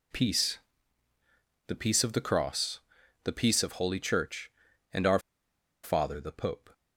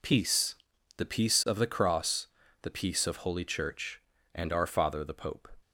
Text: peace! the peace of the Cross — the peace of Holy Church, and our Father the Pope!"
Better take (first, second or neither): second